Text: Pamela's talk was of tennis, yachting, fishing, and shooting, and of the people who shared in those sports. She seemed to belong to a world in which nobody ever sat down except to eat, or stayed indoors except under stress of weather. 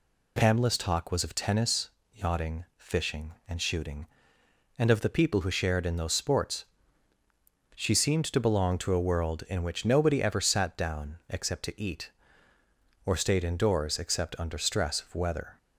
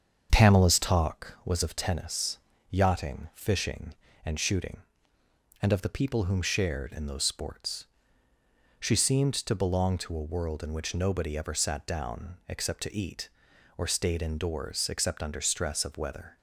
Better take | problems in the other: first | starts louder than the rest; strong; until 1.3 s; 7 dB // says "whom" for "who"; at 6.2 s

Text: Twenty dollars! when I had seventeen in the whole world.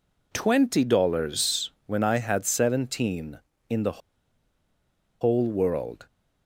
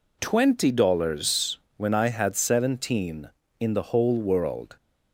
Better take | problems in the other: second | pauses between "the" and "whole"; at 4.0 s; 1.2 s long

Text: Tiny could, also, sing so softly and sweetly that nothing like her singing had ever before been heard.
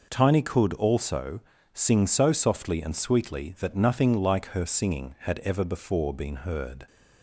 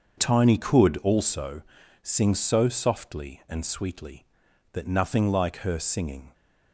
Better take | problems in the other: first | starts louder than the rest; until 1.2 s; 6.5 dB // stops before "had ever before been heard"; at 6.3 s

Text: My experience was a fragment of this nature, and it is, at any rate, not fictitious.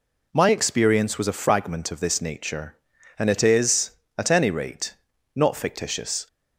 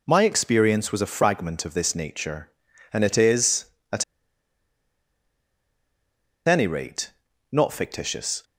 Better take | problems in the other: first | pauses between "at" and "any"; strong; at 4.0 s; 2.4 s long

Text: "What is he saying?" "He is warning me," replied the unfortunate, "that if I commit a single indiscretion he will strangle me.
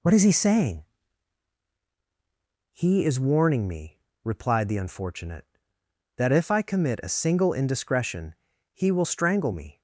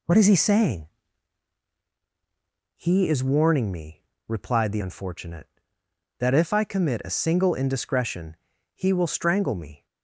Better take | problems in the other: neither | pauses between "indiscretion" and "he"; the same in both

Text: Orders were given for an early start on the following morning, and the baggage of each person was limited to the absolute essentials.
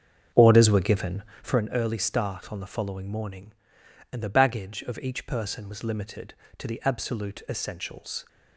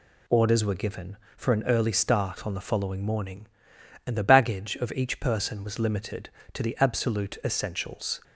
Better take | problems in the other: second | starts louder than the rest; strong; until 1.6 s; 7.5 dB

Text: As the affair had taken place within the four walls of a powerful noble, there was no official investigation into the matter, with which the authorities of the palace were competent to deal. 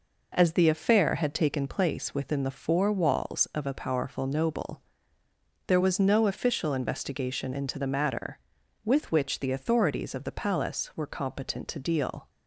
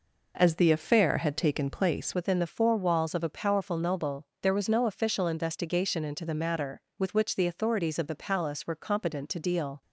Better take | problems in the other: first | changes voice at "within"; from 2.1 s on; 7.7 s long

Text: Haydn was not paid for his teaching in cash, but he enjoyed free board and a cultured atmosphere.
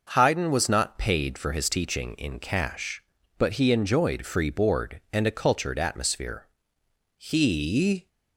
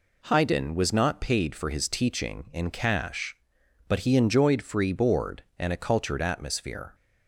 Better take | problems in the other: second | goes on to say "He"; noticeable; from 7.1 s on; 0.90 s long

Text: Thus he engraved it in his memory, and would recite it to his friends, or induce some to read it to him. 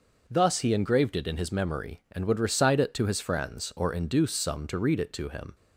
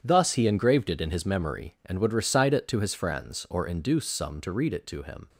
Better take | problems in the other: first | gets quieter; strong; throughout; 11.5 dB

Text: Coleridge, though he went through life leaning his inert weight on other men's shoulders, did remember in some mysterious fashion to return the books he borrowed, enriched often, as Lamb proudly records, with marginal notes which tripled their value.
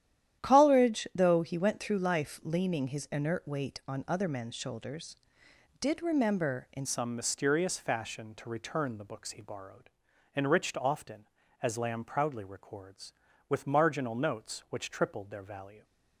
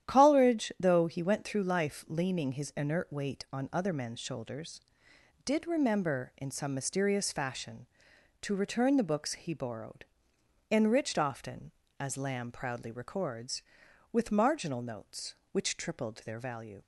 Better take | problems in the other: second | starts louder than the rest; strong; until 1.4 s; 11 dB; strong in the second // changes voice at "some"; from 6.8 s on; 9.0 s long

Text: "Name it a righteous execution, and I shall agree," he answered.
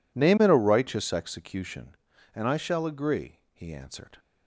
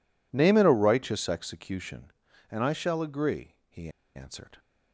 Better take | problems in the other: first | pauses between "he" and "answered"; slight; at 3.8 s; 0.27 s long

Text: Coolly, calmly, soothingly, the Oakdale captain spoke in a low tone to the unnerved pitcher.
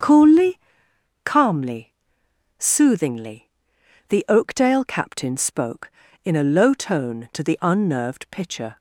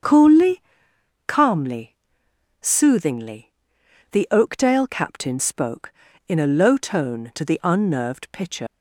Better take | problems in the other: first | starts louder than the rest; strong; until 1.6 s; 7 dB; strong in the first // leaves "pitcher" unfinished; at 8.6 s; 120 ms

